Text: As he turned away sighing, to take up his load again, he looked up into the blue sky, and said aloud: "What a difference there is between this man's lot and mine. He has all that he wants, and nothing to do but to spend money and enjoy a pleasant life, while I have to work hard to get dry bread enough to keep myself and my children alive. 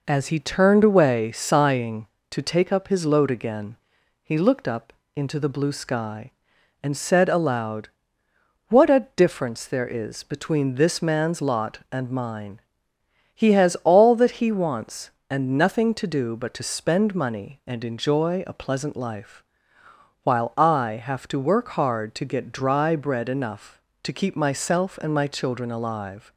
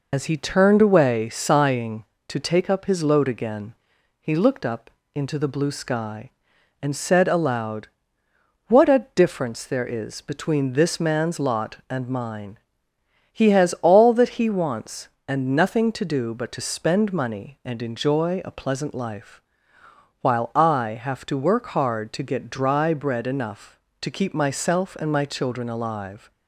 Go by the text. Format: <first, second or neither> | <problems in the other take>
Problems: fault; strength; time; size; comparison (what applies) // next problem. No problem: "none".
first | loses the start of "As"; at 0.1 s; 85 ms // pauses between "up" and "into"; slight; at 4.9 s; 0.24 s long; slight in the first